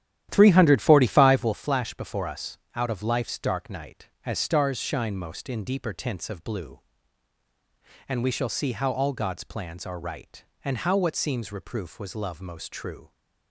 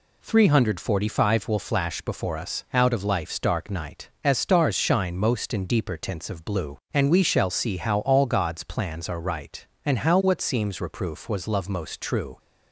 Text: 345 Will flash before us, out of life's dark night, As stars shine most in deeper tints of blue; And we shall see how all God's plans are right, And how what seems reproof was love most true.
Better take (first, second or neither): second